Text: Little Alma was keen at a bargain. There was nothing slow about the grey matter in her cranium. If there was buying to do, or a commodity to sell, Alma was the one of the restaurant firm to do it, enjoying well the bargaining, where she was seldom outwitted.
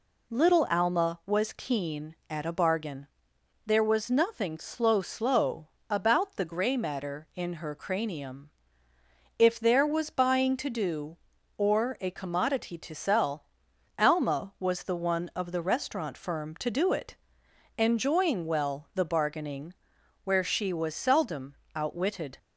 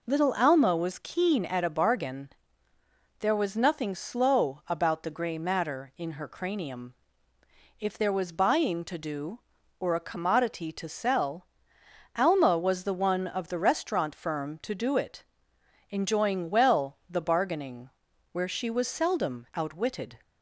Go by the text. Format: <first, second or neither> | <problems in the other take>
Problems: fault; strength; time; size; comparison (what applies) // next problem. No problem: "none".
second | says "slow" twice; at 4.9 s // pauses between "seldom" and "outwitted"; slight; at 21.5 s; 0.18 s long